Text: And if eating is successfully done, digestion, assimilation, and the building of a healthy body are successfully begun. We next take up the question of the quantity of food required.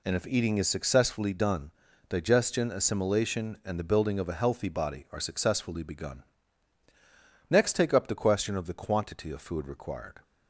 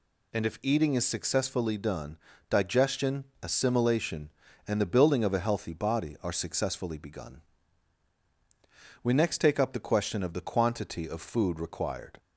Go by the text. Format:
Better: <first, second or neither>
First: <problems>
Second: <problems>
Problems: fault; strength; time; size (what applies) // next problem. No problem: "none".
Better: second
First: skips "We"; at 6.8 s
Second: none